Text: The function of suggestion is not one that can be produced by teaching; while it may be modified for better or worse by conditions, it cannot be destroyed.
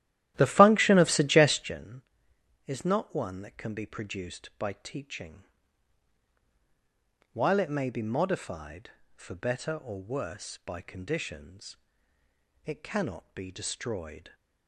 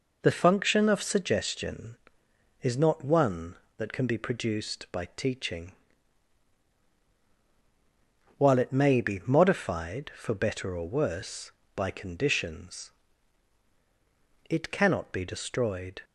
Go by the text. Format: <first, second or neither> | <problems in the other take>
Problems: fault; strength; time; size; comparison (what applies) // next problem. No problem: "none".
second | starts louder than the rest; strong; until 1.8 s; 13 dB